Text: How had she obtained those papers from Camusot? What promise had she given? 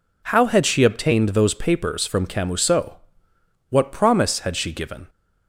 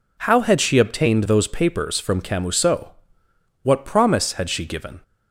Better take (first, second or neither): neither